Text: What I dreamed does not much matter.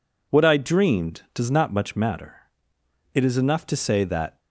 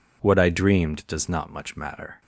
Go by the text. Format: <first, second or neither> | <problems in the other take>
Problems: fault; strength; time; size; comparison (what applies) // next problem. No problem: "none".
second | goes on to say "It is enough to say that"; noticeable; from 3.1 s on; 1.2 s long